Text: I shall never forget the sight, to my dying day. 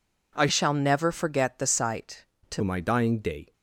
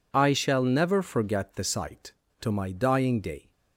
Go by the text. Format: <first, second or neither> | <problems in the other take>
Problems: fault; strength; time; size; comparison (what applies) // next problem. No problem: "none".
second | changes voice from "shall" to "to"; from 0.4 to 2.6 s; 2.2 s long